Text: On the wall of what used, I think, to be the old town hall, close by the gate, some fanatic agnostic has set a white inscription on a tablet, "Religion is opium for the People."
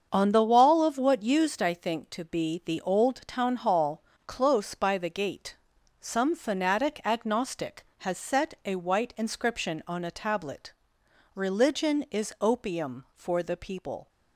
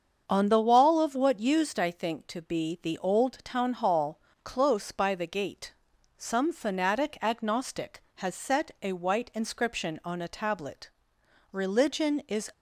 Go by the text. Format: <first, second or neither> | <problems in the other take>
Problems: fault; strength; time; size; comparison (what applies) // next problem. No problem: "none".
first | starts louder than the rest; until 1.2 s; 7 dB; also in the first // stops before "opium for the People"; at 12.5 s